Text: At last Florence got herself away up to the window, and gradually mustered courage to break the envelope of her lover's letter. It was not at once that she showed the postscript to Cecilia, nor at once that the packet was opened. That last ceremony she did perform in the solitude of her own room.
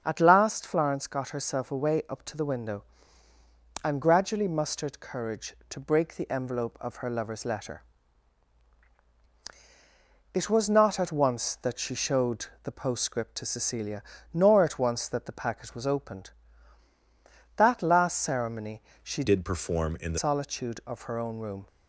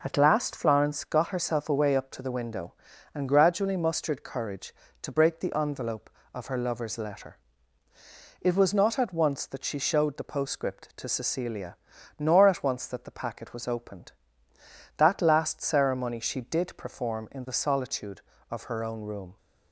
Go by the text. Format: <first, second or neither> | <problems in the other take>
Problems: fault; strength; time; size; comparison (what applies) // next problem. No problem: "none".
second | starts louder than the rest; until 1.0 s; 6.5 dB // pauses between "showed" and "the"; slight; at 12.4 s; 0.18 s long // pauses between "ceremony" and "she"; slight; at 18.8 s; 0.22 s long // changes voice from "did" to "the"; from 19.2 to 20.1 s; 0.9 s long